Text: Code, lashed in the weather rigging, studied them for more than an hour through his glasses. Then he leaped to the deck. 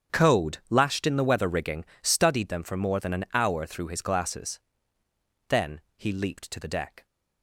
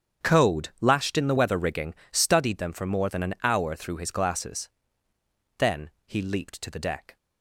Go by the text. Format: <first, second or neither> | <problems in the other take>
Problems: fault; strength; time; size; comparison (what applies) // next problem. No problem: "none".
neither | starts louder than the rest; strong; the same in both // pauses between "Then" and "he"; slight; the same in both